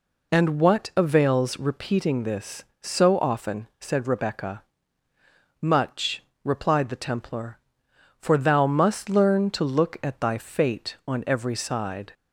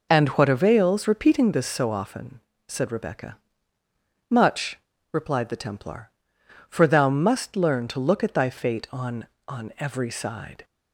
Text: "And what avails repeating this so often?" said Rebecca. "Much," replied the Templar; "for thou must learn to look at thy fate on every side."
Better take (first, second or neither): first